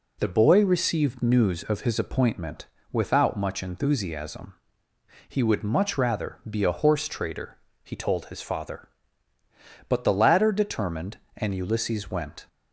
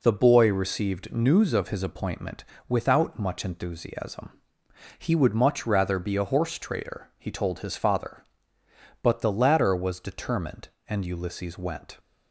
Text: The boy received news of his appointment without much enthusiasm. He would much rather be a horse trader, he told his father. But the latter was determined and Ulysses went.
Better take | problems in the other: second | pauses between "appointment" and "without"; slight; at 2.6 s; 0.24 s long; slight in the second // skips "was"; at 10.5 s

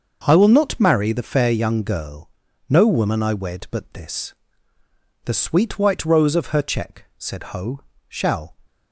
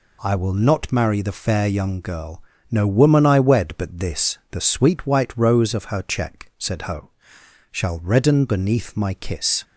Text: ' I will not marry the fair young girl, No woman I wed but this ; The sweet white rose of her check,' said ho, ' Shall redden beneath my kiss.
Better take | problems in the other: second | starts louder than the rest; until 1.2 s; 6.5 dB // stops before "redden beneath my kiss"; at 8.6 s

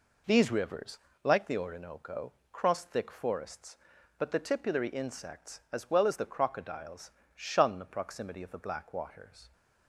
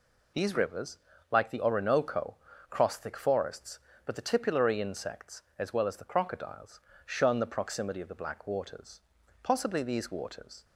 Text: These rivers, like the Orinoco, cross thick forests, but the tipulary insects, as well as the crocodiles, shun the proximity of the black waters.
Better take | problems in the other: first | goes on to say "Possibly these waters"; noticeable; from 9.4 s on; 1.2 s long

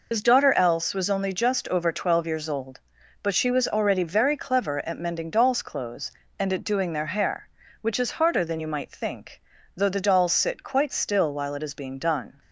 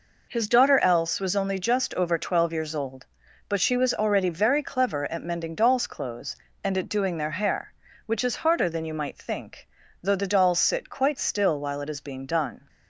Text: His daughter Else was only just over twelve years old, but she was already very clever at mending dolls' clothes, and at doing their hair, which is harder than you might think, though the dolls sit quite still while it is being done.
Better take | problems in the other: second | loses the start of "His"; at 0.1 s; 70 ms

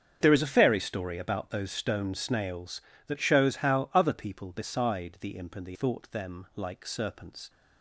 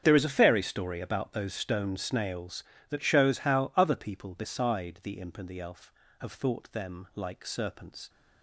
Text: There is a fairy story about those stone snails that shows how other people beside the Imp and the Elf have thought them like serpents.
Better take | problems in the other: second | starts louder than the rest; strong; until 1.2 s; 7 dB; strong in the second // skips "Elf have"; at 5.7 s

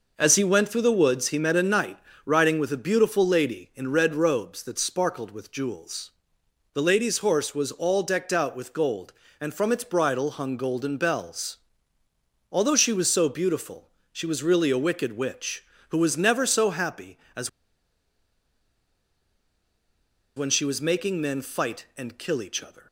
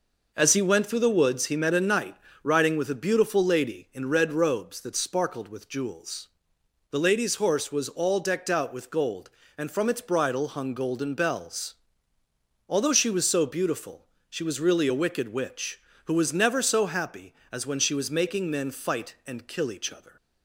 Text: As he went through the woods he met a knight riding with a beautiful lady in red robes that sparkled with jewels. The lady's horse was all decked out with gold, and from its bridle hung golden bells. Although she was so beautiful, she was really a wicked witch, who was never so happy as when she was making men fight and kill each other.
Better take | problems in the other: second | pauses between "knight" and "riding"; slight; at 1.9 s; 0.28 s long; slight in the second // pauses between "as" and "when"; strong; at 17.4 s; 2.8 s long

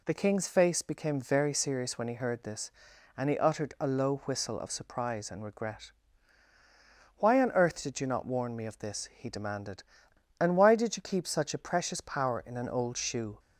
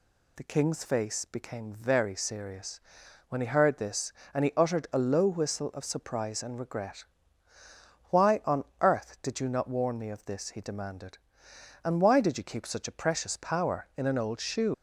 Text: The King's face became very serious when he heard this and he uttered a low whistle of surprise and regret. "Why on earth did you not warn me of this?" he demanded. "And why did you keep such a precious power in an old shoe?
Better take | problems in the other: first | pauses between "serious" and "when"; noticeable; at 2.7 s; 0.48 s long // pauses between "on" and "earth"; slight; at 8.6 s; 0.16 s long // leaves "shoe" unfinished; at 14.7 s; 115 ms

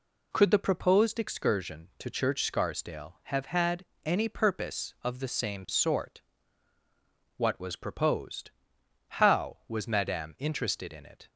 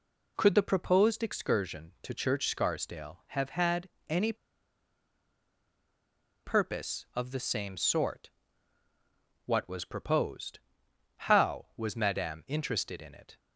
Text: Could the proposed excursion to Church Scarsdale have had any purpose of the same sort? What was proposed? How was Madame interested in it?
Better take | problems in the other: first | pauses between "had" and "any"; slight; at 3.8 s; 0.22 s long; slight in the first // pauses between "any" and "purpose"; strong; at 4.3 s; 2.1 s long

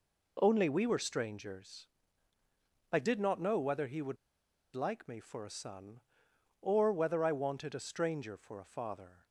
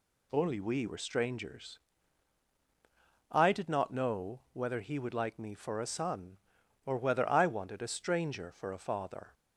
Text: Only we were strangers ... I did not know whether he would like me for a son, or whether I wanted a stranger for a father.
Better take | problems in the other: second | pauses between "would" and "like"; noticeable; at 4.1 s; 0.58 s long

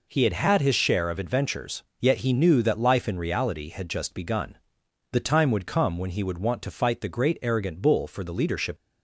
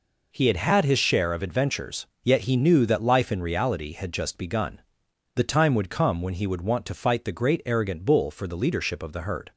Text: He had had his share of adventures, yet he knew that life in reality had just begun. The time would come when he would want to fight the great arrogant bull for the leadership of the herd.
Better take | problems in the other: second | stops before "of the herd"; at 8.7 s

